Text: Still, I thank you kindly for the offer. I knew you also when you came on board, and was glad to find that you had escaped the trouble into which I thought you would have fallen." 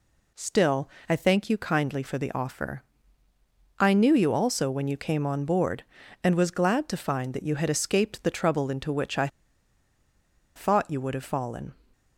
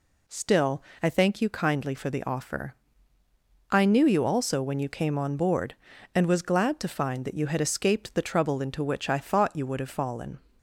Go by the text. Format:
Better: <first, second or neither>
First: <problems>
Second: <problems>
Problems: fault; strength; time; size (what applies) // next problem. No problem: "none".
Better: second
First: pauses between "I" and "thought"; strong; at 9.2 s; 1.2 s long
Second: none